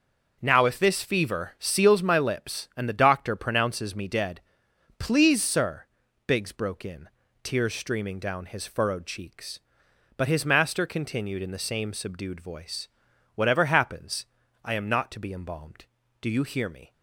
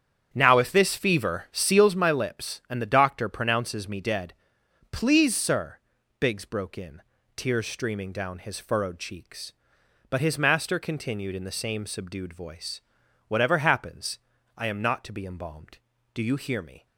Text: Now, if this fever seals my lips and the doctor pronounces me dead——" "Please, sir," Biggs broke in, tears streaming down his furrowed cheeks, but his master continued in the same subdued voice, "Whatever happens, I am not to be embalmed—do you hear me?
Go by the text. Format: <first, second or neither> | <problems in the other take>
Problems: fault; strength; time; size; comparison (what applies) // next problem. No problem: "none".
first | starts louder than the rest; strong; until 1.9 s; 8.5 dB